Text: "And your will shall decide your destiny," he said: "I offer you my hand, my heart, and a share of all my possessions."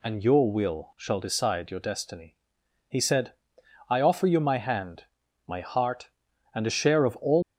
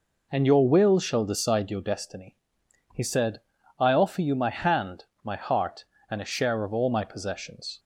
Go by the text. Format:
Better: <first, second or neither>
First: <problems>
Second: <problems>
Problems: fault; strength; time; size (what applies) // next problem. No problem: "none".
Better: second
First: stops before "my possessions"; at 7.4 s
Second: none